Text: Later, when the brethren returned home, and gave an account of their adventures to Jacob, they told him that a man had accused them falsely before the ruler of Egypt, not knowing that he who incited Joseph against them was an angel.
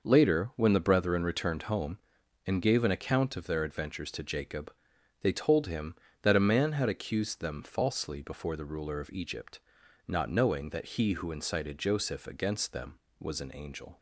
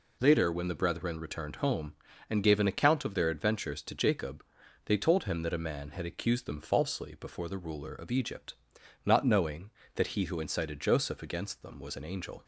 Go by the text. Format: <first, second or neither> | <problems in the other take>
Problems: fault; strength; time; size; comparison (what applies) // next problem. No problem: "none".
neither | none